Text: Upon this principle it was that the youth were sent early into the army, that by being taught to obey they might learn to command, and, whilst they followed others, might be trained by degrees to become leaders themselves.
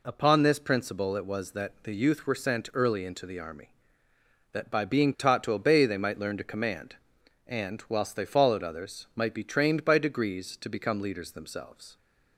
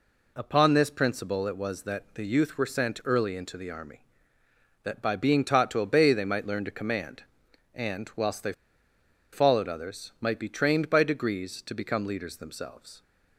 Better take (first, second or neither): first